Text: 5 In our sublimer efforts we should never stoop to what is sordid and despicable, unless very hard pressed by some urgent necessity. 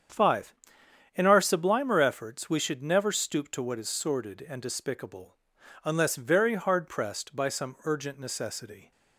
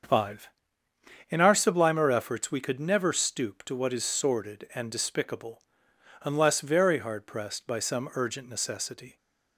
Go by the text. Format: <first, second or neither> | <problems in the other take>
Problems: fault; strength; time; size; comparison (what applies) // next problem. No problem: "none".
first | starts louder than the rest; until 1.8 s; 7 dB; strong in the first // says "could" for "should"; at 2.6 s